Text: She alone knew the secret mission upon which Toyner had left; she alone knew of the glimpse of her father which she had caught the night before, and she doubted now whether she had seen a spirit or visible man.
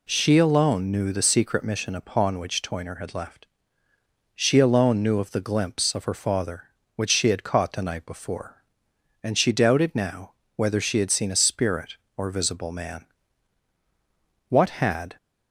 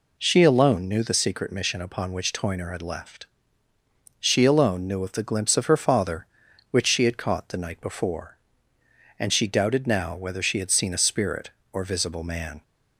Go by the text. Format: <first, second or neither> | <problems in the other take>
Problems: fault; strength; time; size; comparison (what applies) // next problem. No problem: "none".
second | pauses between "now" and "whether"; slight; at 10.3 s; 0.20 s long // goes on to say "What had"; noticeable; from 14.4 s on; 0.68 s long